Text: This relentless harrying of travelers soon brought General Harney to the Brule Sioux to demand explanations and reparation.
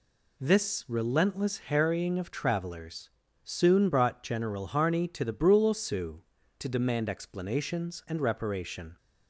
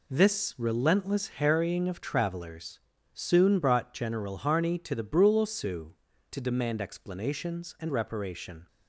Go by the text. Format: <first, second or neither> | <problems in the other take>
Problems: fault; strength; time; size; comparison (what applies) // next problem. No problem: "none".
first | gets quieter; strong; throughout; 8 dB // pauses between "travelers" and "soon"; slight; at 2.7 s; 0.34 s long; slight in the first